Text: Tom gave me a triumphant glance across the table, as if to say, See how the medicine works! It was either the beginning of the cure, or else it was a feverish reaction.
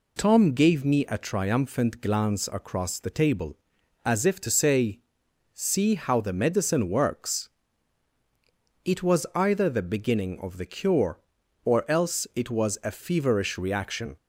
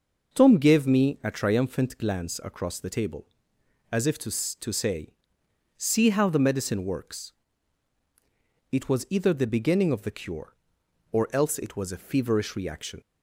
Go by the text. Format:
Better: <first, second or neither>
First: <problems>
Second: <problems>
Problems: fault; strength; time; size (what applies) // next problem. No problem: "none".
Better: first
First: none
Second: says "to" twice; at 4.6 s